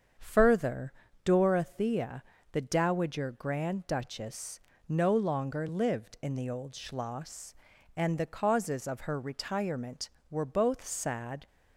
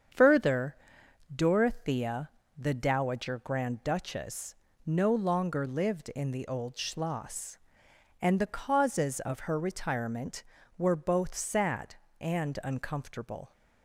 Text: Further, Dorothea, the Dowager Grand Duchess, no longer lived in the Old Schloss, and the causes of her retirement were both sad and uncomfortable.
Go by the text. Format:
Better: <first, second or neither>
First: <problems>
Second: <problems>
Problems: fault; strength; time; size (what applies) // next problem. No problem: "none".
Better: second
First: starts louder than the rest; strong; until 1.5 s; 7 dB // stops before "and uncomfortable"; at 11.4 s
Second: starts louder than the rest; strong; until 1.7 s; 7.5 dB